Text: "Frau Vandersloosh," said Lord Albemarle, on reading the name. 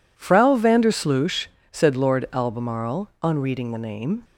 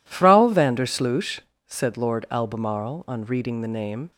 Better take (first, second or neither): neither